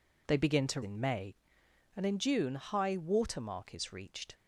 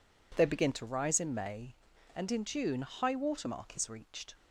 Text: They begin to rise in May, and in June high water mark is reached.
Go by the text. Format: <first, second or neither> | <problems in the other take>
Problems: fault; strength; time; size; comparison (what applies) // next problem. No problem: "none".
second | skips "rise"; at 0.8 s